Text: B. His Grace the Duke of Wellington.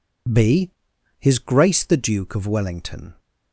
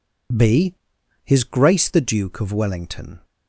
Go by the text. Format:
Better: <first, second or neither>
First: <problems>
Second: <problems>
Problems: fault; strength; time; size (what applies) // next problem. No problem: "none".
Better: neither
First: none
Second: none